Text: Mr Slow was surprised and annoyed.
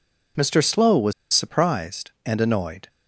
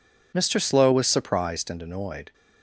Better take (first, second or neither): second